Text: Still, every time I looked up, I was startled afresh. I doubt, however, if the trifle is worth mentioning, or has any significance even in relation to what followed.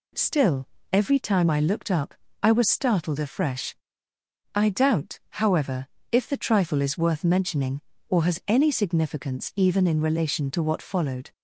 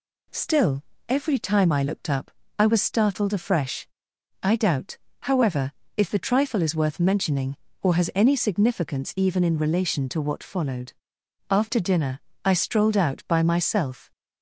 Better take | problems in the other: first | goes on to say "After dinner I strolled out by myself"; strong; from 11.4 s on; 2.6 s long

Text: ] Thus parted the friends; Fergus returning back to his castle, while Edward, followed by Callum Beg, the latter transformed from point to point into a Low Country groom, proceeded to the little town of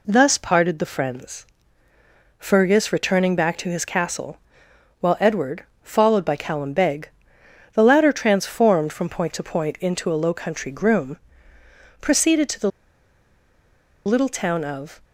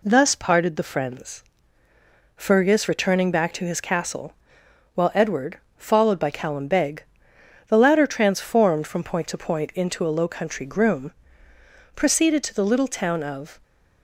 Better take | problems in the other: second | pauses between "the" and "little"; strong; at 12.6 s; 1.3 s long

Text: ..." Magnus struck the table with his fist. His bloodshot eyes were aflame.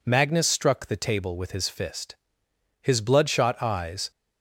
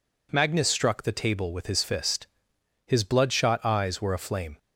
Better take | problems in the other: second | stops before "were aflame"; at 4.1 s

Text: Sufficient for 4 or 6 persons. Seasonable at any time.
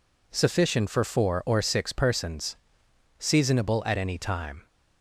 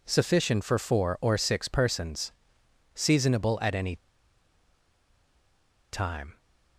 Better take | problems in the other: first | pauses between "any" and "time"; strong; at 3.9 s; 1.9 s long

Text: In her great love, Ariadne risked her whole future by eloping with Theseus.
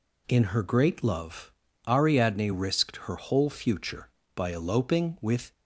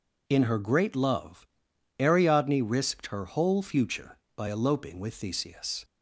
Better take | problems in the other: second | stops before "Theseus"; at 5.5 s

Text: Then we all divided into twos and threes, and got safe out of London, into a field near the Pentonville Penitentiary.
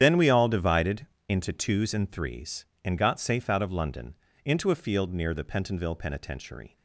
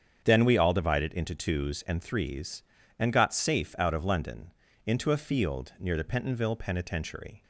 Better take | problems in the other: second | loses the start of "Then"; at 0.0 s; 80 ms // starts louder than the rest; strong; until 1.0 s; 9.5 dB; strong in the second // pauses between "divided" and "into"; slight; at 1.0 s; 0.22 s long

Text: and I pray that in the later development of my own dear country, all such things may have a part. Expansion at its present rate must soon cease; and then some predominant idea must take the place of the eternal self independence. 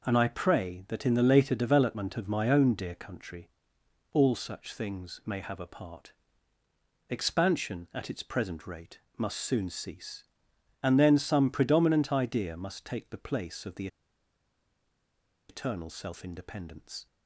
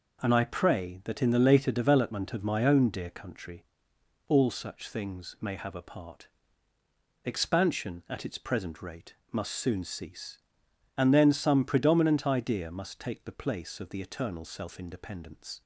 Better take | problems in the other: second | pauses between "rate" and "must"; slight; at 8.9 s; 0.18 s long; slight in the second // pauses between "the" and "eternal"; strong; at 13.8 s; 1.6 s long

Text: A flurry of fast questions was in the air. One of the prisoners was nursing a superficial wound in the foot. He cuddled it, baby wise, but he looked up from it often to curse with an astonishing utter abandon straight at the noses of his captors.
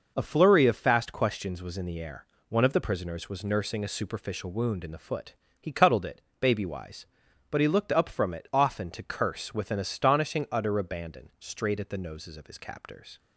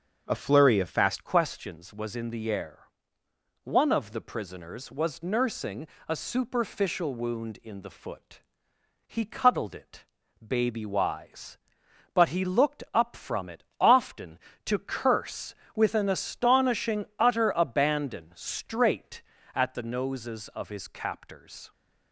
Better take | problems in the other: first | starts louder than the rest; until 1.2 s; 6.5 dB // changes voice at "questions"; from 1.2 s on; 20.5 s long // pauses between "nursing" and "a"; slight; at 5.8 s; 0.22 s long // pauses between "it" and "often"; slight; at 13.6 s; 0.16 s long

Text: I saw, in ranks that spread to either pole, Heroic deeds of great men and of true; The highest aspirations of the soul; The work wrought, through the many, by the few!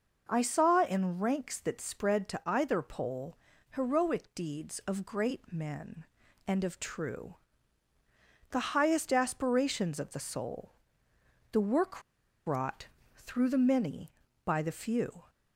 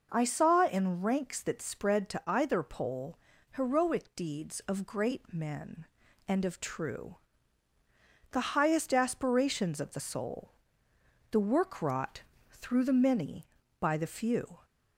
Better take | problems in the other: second | pauses between "work" and "wrought"; at 12.0 s; 0.45 s long

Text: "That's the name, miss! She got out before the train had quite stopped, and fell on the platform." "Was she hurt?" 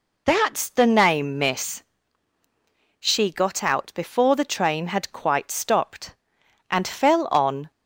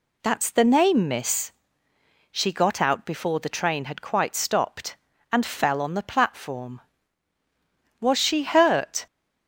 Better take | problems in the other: second | stops before "the platform Was she hurt"; at 7.7 s

